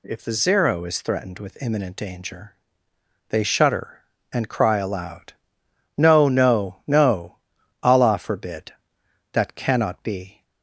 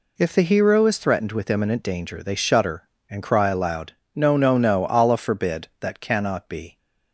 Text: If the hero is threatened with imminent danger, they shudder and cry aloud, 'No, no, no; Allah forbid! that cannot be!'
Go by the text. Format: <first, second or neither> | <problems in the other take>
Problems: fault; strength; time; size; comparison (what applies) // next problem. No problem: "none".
second | says "zero" for "hero"; at 0.3 s